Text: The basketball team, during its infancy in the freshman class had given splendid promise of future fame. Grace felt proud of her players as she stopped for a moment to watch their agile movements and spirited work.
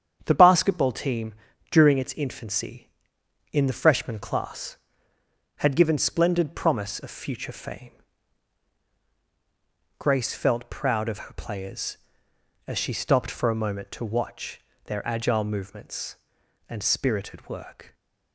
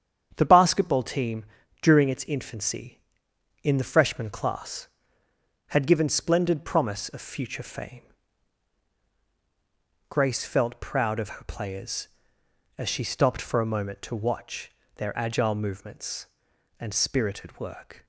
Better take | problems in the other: neither | starts louder than the rest; strong; the same in both // pauses between "watch" and "their"; slight; the same in both

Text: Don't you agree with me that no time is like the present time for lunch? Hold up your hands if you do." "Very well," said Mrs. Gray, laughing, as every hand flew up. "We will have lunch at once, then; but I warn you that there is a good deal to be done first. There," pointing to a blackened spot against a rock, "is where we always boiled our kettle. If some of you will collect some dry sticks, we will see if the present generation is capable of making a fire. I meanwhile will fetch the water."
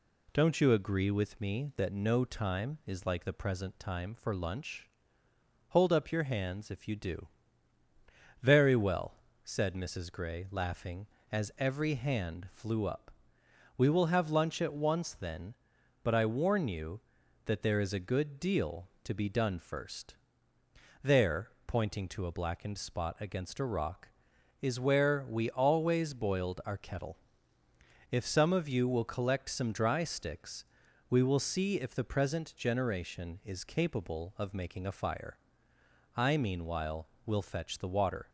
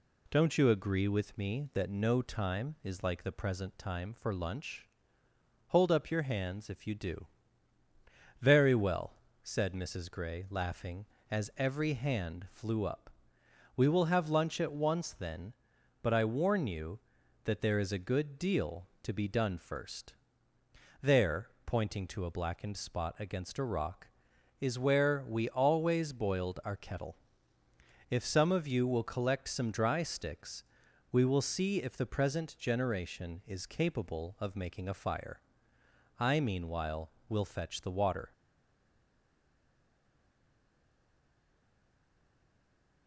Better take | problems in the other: first | stays silent after the last word; strong; from 38.3 s on; 4.7 s long

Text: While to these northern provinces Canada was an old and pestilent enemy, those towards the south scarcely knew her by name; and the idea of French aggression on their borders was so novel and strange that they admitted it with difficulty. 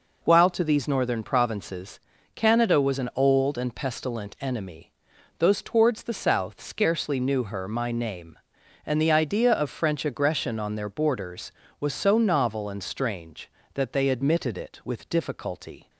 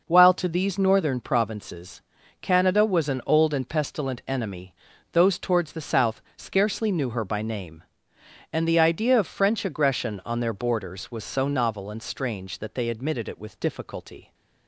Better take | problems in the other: second | pauses between "provinces" and "Canada"; at 1.9 s; 0.38 s long; also in the second // says "my" for "by"; at 7.6 s

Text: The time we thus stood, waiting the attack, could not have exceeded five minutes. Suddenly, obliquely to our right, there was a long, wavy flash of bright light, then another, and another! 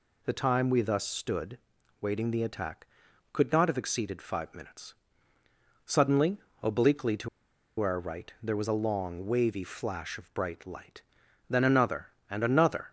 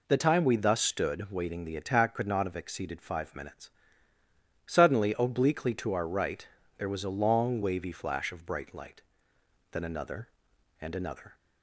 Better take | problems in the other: second | pauses between "to" and "our"; noticeable; at 7.2 s; 0.51 s long

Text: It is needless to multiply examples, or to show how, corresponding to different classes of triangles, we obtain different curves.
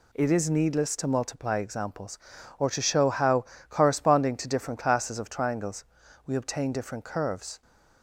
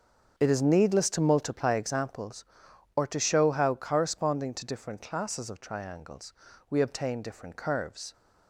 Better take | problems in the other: first | starts louder than the rest; until 2.2 s; 6.5 dB

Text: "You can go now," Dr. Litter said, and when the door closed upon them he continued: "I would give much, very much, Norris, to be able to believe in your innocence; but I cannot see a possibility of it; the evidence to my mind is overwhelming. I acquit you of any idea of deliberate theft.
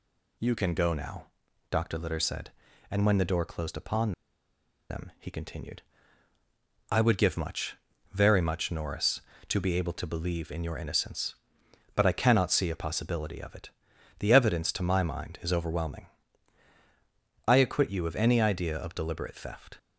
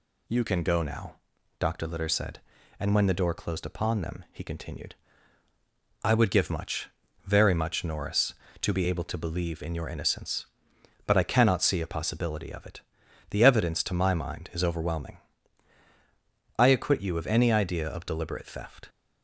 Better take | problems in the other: second | pauses between "upon" and "them"; noticeable; at 4.1 s; 0.78 s long

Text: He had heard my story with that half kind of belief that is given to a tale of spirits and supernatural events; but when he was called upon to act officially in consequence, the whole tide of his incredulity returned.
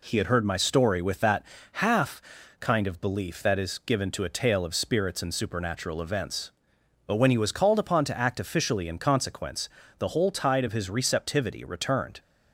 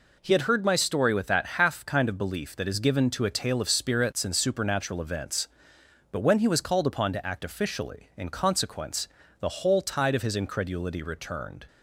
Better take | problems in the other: second | pauses between "that" and "half"; slight; at 1.4 s; 0.28 s long // pauses between "half" and "kind"; at 2.2 s; 0.38 s long // says "receptivity" for "incredulity"; at 10.8 s

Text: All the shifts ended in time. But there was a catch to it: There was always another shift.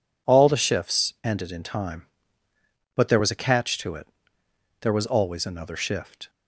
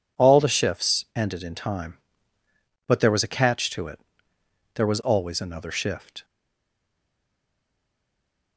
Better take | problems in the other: first | stays silent after the last word; from 6.2 s on; 2.3 s long

